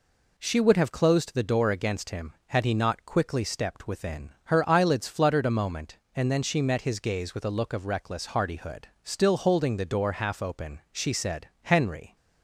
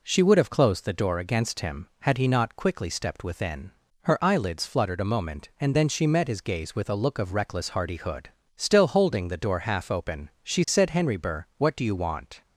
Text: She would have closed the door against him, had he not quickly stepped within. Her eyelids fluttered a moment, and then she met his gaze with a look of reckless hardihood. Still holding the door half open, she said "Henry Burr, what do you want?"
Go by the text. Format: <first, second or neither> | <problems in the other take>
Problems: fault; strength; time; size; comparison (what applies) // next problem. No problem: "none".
second | pauses between "said" and "Henry"; slight; at 11.4 s; 0.16 s long // stops before "Burr what do you want"; at 12.1 s